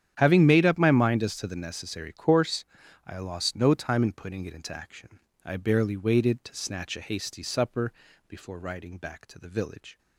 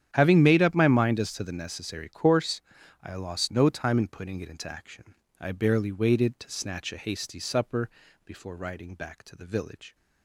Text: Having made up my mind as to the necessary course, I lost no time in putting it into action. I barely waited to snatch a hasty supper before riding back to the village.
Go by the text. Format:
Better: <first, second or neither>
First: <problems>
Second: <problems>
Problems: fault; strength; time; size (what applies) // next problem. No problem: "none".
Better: neither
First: starts louder than the rest; strong; until 1.1 s; 9.5 dB // pauses between "supper" and "before"; slight; at 7.9 s; 0.34 s long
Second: starts louder than the rest; strong; until 1.1 s; 9.5 dB // pauses between "supper" and "before"; slight; at 7.9 s; 0.34 s long